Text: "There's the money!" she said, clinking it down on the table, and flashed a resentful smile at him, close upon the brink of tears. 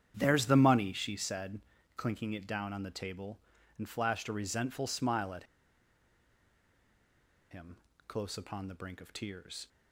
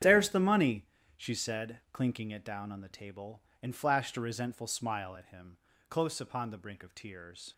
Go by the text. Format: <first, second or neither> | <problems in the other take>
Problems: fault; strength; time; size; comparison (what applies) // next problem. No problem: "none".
second | starts louder than the rest; strong; until 1.1 s; 9 dB; strong in the second // pauses between "at" and "him"; strong; at 5.4 s; 2.0 s long